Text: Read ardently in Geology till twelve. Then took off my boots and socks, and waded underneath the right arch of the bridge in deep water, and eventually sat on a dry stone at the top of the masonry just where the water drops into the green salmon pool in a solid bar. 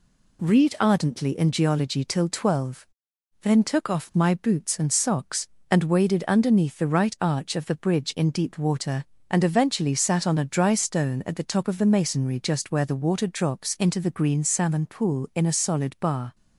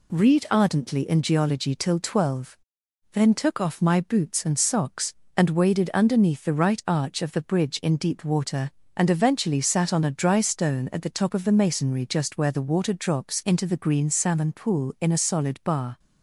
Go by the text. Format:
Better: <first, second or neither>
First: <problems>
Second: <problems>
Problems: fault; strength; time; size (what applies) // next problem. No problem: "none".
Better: neither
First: none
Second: none